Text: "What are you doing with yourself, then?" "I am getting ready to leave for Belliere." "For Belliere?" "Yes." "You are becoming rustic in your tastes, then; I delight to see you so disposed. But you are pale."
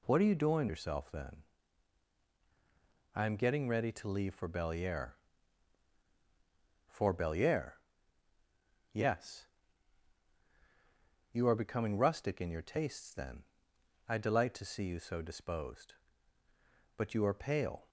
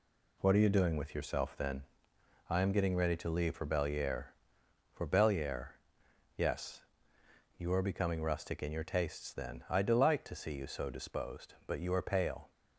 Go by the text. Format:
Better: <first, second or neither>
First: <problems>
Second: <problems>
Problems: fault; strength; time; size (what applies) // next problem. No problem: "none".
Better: second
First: skips "with"; at 0.6 s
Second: none